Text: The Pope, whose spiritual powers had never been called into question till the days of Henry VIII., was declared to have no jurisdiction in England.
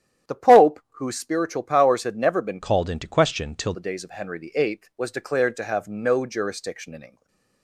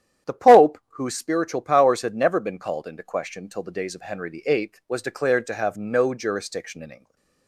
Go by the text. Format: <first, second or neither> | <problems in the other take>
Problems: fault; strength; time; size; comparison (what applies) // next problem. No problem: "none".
second | starts louder than the rest; strong; until 1.4 s; 10.5 dB; strong in the second // changes voice from "called" to "till"; from 2.6 to 3.7 s; 1.1 s long // stays silent after the last word; slight; from 7.0 s on; 0.6 s long; slight in the second